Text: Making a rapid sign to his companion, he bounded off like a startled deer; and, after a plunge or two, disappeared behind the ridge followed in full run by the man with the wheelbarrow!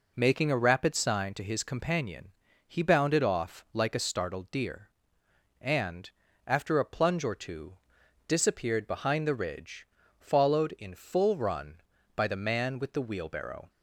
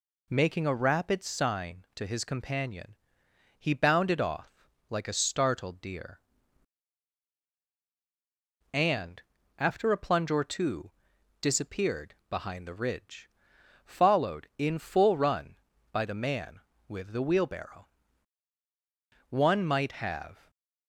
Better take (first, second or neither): first